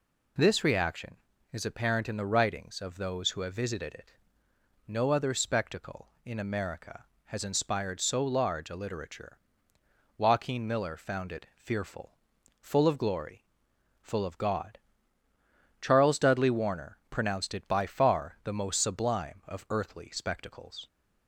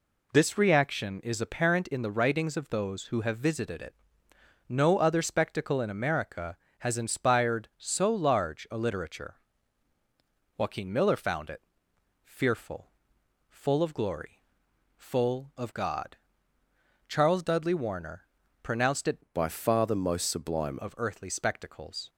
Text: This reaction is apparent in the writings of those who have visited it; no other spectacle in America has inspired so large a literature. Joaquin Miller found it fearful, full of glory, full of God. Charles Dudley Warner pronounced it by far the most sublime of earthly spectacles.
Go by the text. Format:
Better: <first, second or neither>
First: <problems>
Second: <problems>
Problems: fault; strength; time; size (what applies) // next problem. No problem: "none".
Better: first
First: none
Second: pauses between "it" and "fearful"; noticeable; at 11.6 s; 0.60 s long // pauses between "Warner" and "pronounced"; slight; at 18.2 s; 0.34 s long // changes voice from "by" to "sublime"; from 19.3 to 20.7 s; 1.4 s long